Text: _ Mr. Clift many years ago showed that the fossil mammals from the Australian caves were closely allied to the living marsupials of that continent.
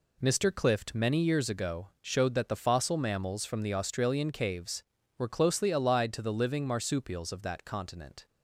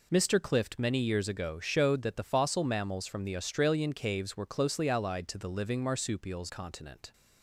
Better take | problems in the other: first | skips "of that"; at 6.4 s

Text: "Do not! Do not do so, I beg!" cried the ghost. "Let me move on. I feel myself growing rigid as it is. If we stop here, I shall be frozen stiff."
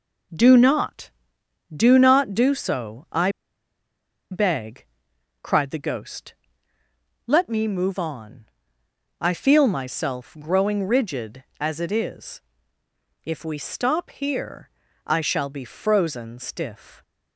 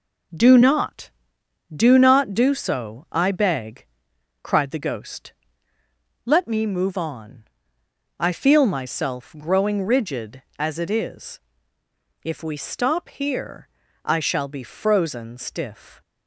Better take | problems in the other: second | pauses between "I" and "beg"; at 3.3 s; 1.0 s long

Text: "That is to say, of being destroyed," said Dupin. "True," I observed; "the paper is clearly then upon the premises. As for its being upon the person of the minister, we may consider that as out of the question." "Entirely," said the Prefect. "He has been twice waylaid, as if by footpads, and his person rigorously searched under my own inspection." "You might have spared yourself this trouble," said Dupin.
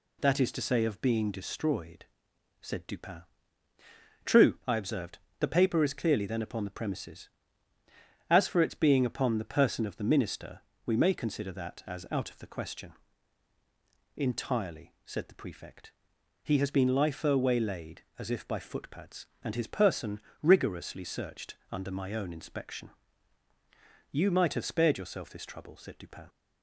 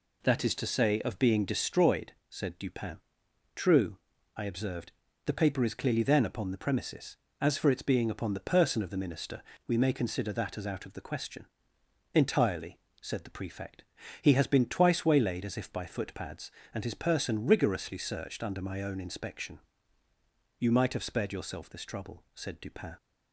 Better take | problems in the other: second | says "lifer" for "twice"; at 16.9 s // pauses between "person" and "rigorously"; slight; at 20.2 s; 0.22 s long // pauses between "searched" and "under"; slight; at 21.5 s; 0.16 s long

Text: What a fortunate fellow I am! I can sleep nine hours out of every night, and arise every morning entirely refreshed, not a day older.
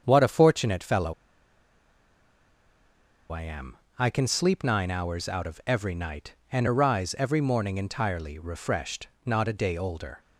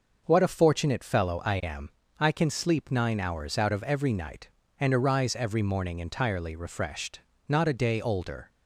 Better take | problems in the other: second | starts louder than the rest; strong; until 1.0 s; 7.5 dB // pauses between "fellow" and "I"; strong; at 1.1 s; 2.1 s long

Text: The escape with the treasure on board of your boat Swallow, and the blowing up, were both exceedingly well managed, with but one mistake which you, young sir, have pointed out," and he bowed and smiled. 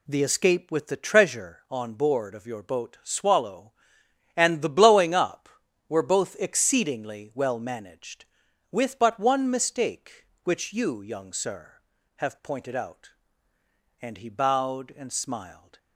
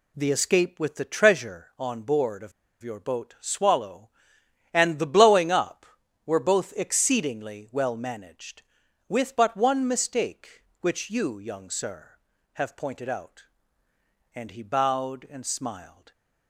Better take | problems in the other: first | pauses between "of" and "your"; slight; at 2.5 s; 0.31 s long

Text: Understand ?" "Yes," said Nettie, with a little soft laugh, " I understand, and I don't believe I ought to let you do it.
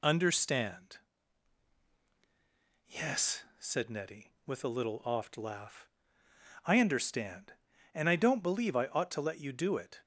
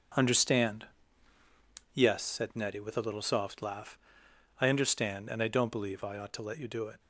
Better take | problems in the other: second | says "oft" for "soft"; at 5.0 s

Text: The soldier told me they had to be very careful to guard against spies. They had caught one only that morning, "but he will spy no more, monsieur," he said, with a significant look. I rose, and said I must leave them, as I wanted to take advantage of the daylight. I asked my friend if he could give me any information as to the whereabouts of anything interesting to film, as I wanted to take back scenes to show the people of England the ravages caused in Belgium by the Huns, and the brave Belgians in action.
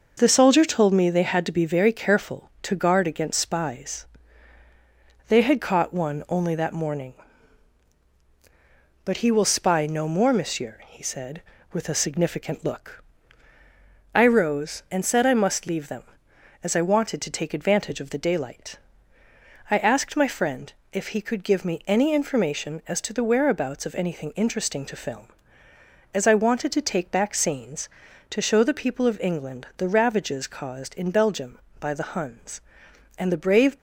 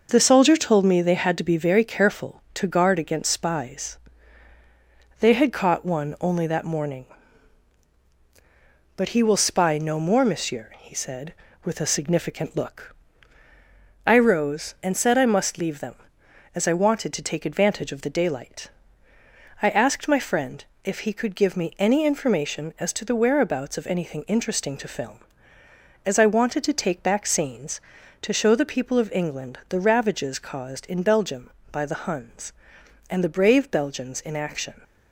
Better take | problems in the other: second | pauses between "friend" and "if"; slight; at 20.7 s; 0.20 s long; slight in the second // stops before "Belgians in action"; at 33.7 s

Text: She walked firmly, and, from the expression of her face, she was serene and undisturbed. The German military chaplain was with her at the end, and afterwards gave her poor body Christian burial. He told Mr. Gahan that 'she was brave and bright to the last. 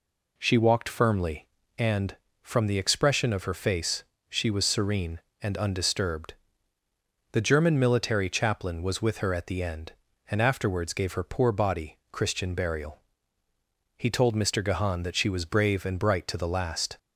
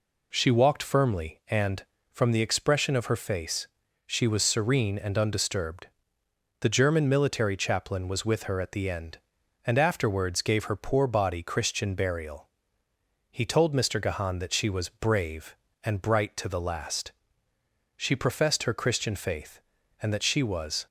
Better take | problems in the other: first | goes on to say "She professed her Christian faith and that she was"; strong; from 17.9 s on; 2.9 s long

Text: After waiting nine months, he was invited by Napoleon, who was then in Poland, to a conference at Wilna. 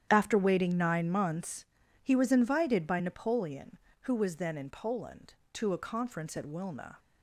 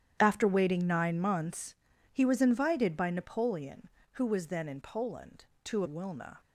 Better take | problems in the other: first | starts louder than the rest; strong; until 1.2 s; 10 dB; strong in the first // skips "a conference at"; at 5.8 s

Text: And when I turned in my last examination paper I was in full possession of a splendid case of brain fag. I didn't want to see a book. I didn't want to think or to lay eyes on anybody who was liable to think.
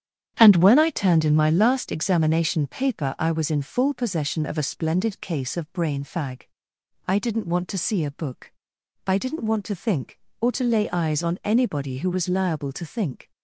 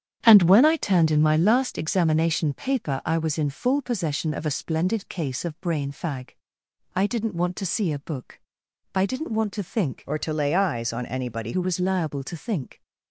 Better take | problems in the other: first | starts louder than the rest; strong; until 1.2 s; 9 dB; strong in the first // changes voice from "or" to "anybody"; from 10.0 to 11.5 s; 1.5 s long

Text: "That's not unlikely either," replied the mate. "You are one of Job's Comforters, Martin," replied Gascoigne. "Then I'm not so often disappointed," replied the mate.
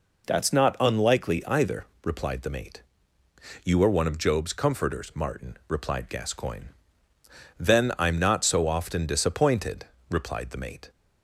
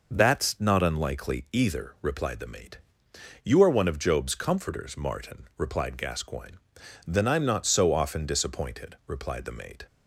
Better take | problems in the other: neither | none

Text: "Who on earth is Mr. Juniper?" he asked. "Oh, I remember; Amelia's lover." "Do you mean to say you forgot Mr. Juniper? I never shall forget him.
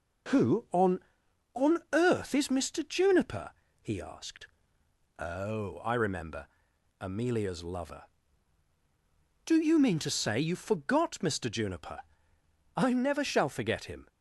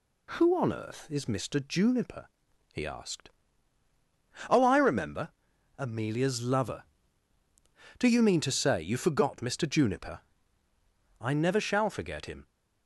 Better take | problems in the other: second | says "on" twice; at 1.5 s

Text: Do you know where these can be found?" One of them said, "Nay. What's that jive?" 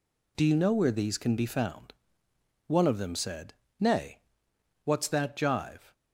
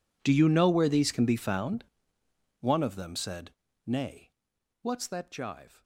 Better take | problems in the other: first | gets quieter; strong; throughout; 21.5 dB

